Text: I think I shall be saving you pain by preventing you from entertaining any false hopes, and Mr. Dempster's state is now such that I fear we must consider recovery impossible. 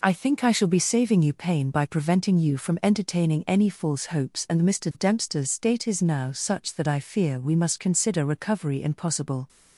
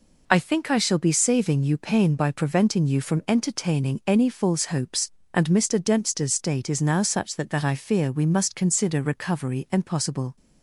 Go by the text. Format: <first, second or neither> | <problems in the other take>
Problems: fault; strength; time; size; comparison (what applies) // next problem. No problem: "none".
first | says "that" twice; at 7.4 s